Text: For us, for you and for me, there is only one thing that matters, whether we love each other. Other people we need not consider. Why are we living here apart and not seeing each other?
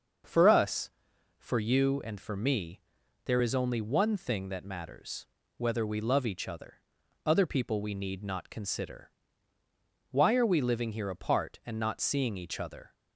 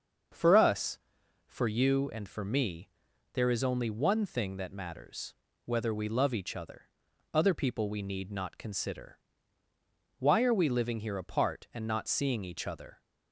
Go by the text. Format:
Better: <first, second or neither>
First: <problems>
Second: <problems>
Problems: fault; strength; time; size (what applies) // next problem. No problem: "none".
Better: neither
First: starts louder than the rest; noticeable; until 1.7 s; 6 dB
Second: starts louder than the rest; until 1.8 s; 6.5 dB